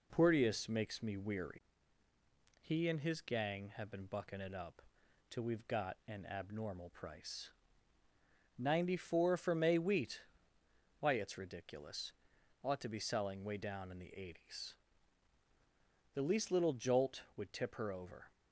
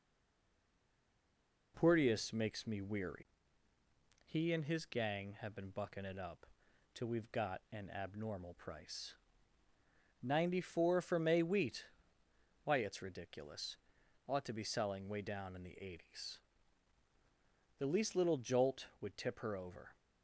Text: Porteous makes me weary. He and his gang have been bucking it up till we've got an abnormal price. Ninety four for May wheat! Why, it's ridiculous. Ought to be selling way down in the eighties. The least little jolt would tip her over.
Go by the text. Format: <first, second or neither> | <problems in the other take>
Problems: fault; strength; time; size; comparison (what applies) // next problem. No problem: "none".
first | stays silent before the first word; noticeable; until 1.7 s; 1.7 s long // pauses between "up" and "till"; noticeable; at 6.4 s; 0.48 s long; noticeable in the first